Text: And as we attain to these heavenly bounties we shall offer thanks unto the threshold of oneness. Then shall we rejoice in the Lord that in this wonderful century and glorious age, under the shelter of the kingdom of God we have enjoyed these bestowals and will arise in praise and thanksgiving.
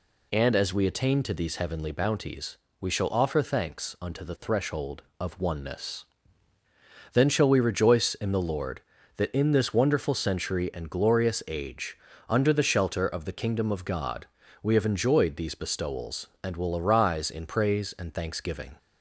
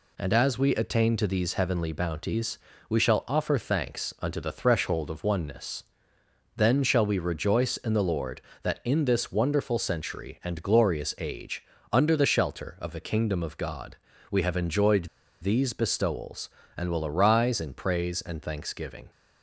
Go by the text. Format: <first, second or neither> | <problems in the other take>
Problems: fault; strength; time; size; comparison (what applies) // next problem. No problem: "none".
first | pauses between "bounties" and "we"; slight; at 2.5 s; 0.32 s long; slight in the first // pauses between "God" and "we"; slight; at 13.9 s; 0.34 s long; slight in the first // pauses between "enjoyed" and "these"; slight; at 15.0 s; 0.36 s long